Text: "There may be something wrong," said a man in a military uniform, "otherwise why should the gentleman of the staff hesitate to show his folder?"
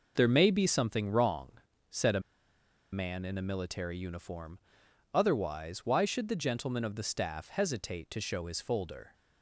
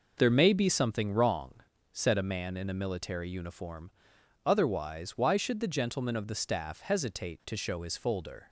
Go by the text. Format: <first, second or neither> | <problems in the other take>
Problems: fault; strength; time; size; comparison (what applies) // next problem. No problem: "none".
second | pauses between "a" and "man"; noticeable; at 2.2 s; 0.70 s long